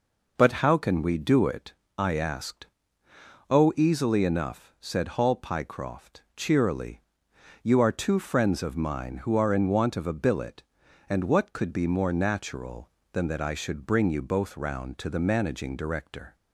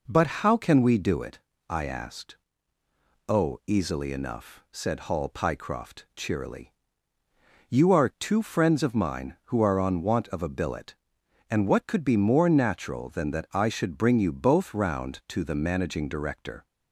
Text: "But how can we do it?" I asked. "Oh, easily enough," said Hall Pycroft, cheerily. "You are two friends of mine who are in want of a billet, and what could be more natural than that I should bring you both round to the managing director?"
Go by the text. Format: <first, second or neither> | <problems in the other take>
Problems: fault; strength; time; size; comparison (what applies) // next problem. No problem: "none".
first | says "on" for "in"; at 9.8 s